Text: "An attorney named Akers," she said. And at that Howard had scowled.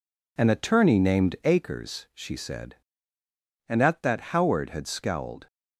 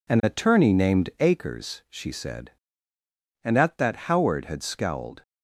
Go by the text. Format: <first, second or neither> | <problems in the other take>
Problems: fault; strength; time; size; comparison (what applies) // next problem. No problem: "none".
neither | none